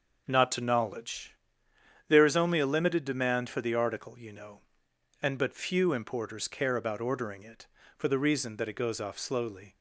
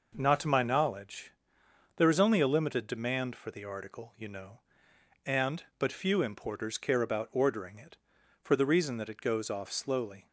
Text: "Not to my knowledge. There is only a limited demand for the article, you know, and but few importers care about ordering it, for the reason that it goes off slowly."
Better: second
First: skips "my"; at 0.6 s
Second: none

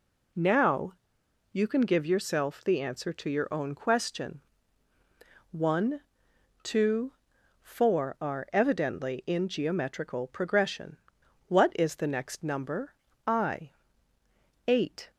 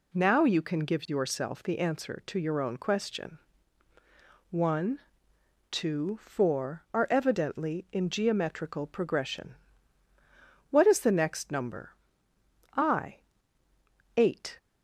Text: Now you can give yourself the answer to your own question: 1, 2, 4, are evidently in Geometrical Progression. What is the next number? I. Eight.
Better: second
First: pauses between "Now" and "you"; noticeable; at 0.9 s; 0.59 s long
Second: none

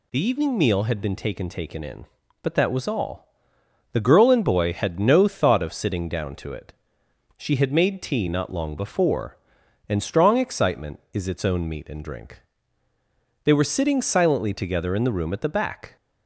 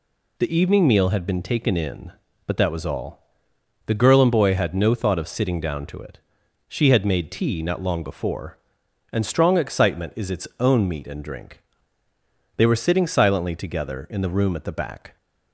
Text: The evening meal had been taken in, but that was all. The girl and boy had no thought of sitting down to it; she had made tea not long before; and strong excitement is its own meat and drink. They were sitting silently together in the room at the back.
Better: second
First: says "taken" twice; at 1.4 s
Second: none

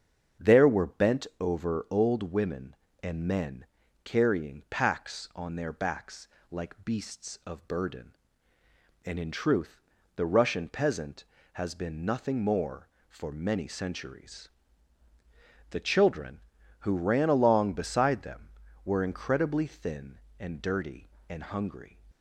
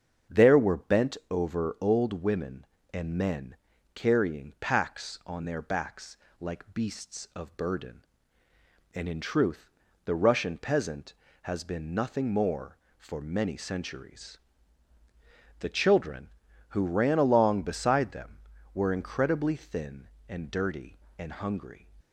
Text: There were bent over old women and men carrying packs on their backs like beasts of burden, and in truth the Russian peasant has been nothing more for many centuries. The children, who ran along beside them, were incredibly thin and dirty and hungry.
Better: neither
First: starts louder than the rest; strong; until 1.5 s; 7.5 dB // pauses between "men" and "carrying"; at 3.6 s; 0.38 s long // pauses between "backs" and "like"; slight; at 6.2 s; 0.24 s long // pauses between "truth" and "the"; slight; at 9.8 s; 0.34 s long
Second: starts louder than the rest; strong; until 1.4 s; 7.5 dB // pauses between "men" and "carrying"; at 3.5 s; 0.38 s long // pauses between "backs" and "like"; slight; at 6.1 s; 0.24 s long // pauses between "truth" and "the"; slight; at 9.7 s; 0.34 s long

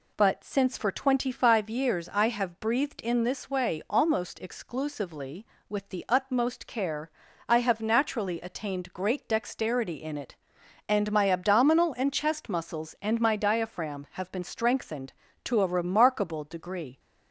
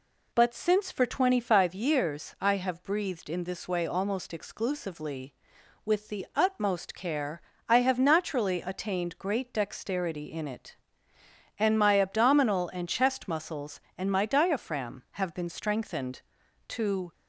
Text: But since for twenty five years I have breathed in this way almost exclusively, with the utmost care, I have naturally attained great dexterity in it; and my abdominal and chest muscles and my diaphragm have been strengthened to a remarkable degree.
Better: first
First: none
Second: stops before "a remarkable degree"; at 17.1 s

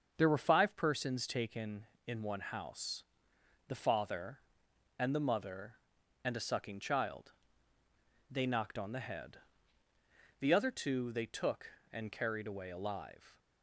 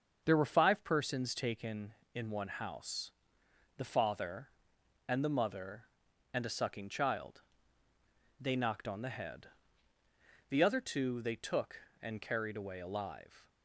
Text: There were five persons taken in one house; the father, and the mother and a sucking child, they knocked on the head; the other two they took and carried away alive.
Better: neither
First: starts louder than the rest; until 1.1 s; 6.5 dB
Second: starts louder than the rest; until 1.2 s; 6.5 dB

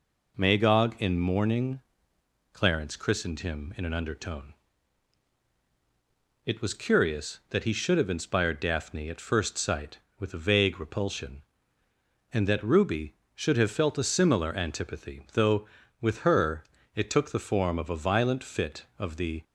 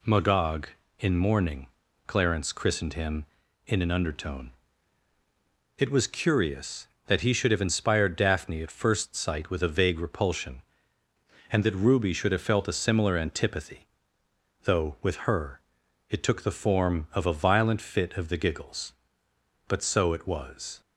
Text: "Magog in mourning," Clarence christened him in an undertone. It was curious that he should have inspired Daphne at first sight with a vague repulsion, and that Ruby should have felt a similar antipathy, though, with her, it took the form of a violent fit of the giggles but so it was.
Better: second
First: stops before "giggles but so it was"; at 19.4 s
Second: none

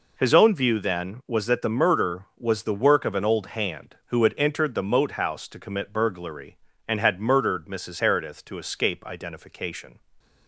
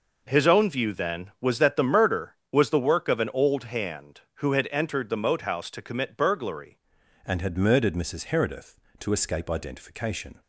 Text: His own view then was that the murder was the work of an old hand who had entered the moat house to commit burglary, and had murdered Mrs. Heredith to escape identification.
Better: first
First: none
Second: changes voice at "and"; from 7.2 s on; 3.2 s long

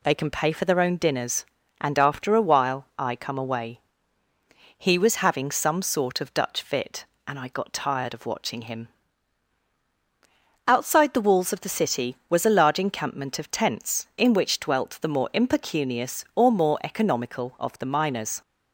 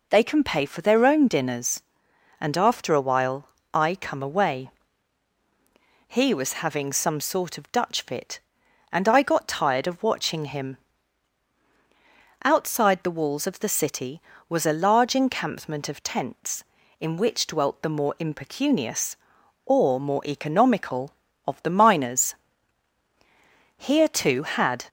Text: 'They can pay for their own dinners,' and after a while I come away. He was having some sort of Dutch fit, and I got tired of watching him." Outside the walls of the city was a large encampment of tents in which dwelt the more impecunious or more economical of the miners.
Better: first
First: none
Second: pauses between "while" and "I"; slight; at 3.4 s; 0.24 s long // goes on to say "Here too had"; noticeable; from 23.7 s on; 1.1 s long

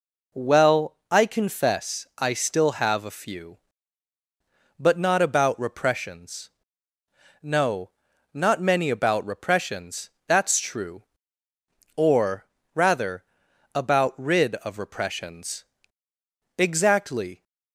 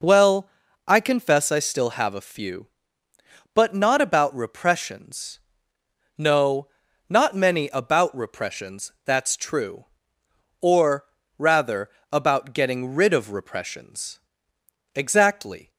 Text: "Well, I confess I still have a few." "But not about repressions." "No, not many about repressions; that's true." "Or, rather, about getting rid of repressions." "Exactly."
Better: second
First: skips "getting"; at 14.1 s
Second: none

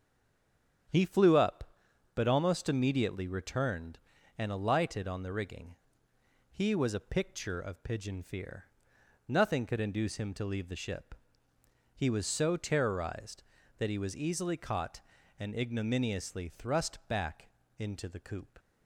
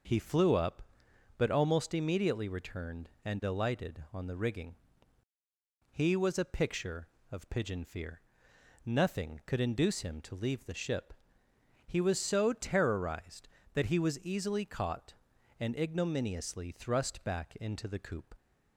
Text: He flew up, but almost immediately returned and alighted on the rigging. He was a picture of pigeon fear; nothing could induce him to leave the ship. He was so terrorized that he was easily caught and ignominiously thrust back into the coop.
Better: second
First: stays silent before the first word; slight; until 0.8 s; 0.8 s long // starts louder than the rest; strong; until 2.4 s; 9 dB // pauses between "back" and "into"; slight; at 17.4 s; 0.30 s long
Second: none

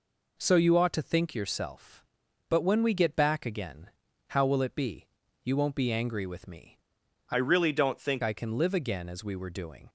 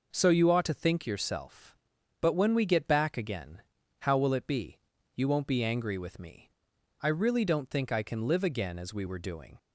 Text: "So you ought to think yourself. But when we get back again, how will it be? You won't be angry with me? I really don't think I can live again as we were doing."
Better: second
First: changes voice from "really" to "think"; from 7.3 to 8.2 s; 0.9 s long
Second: none

